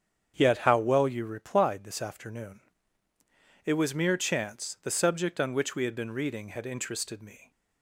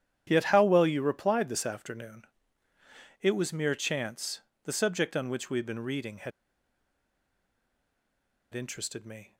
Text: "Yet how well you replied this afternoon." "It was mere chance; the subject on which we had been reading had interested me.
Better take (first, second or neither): first